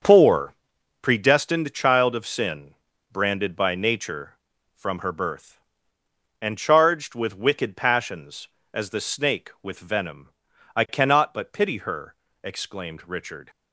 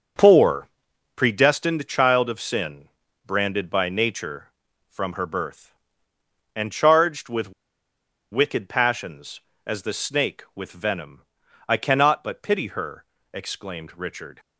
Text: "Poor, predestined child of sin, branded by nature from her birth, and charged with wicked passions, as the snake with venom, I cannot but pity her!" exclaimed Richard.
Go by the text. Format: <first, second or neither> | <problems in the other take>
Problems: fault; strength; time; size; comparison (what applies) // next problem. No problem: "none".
first | starts louder than the rest; until 1.6 s; 6.5 dB; also in the first // pauses between "with" and "wicked"; noticeable; at 7.5 s; 0.80 s long